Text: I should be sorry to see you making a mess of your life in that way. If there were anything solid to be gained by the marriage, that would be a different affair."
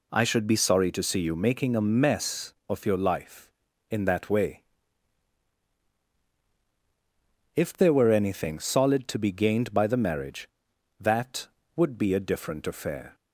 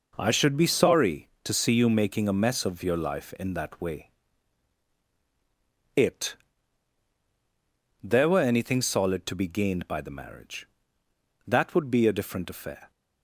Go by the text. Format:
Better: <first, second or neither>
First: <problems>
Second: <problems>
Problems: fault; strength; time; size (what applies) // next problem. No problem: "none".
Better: first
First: none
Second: says "It" for "If"; at 5.9 s